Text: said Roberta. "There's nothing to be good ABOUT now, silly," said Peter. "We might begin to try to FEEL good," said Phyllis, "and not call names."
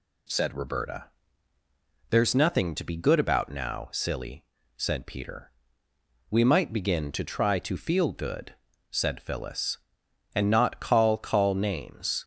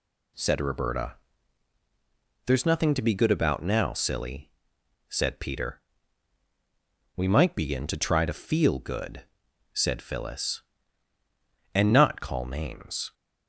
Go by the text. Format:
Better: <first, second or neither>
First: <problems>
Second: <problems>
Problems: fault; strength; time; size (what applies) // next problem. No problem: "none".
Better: second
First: says "call" twice; at 11.1 s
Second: none